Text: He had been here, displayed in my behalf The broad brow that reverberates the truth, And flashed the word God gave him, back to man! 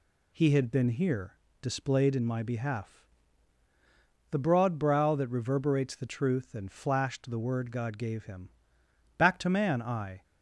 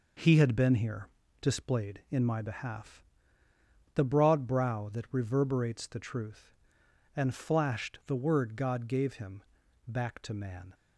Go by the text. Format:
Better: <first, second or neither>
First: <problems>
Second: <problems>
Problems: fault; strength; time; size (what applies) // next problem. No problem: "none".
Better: second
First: pauses between "behalf" and "The"; strong; at 3.0 s; 1.2 s long // goes on to say "I"; slight; from 9.8 s on; 0.40 s long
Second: pauses between "behalf" and "The"; noticeable; at 3.0 s; 0.90 s long